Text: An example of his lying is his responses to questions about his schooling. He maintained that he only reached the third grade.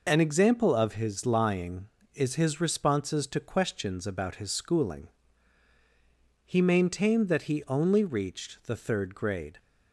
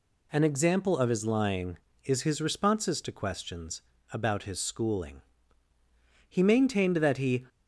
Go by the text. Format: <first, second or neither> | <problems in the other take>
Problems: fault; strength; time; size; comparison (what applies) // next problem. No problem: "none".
first | pauses between "questions" and "about"; slight; at 3.8 s; 0.30 s long // stops before "only reached the third grade"; at 7.4 s